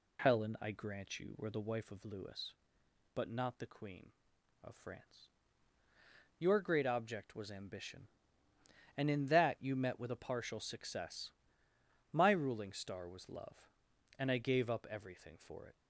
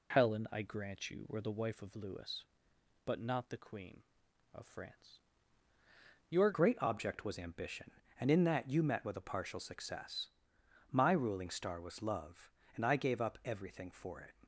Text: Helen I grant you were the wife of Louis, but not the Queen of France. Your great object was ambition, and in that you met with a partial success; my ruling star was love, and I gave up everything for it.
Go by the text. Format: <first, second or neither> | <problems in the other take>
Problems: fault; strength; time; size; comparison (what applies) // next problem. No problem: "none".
first | changes voice at "great"; from 6.5 s on; 7.8 s long